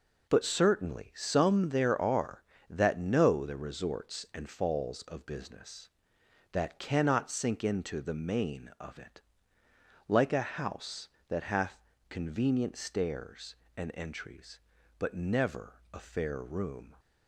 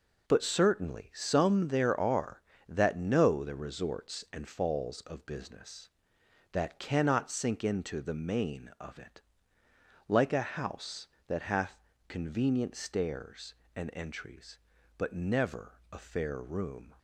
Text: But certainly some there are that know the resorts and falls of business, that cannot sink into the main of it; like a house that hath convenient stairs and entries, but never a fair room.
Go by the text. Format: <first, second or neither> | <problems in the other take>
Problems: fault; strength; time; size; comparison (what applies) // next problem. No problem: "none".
neither | pauses between "hath" and "convenient"; slight; the same in both // pauses between "never" and "a"; slight; the same in both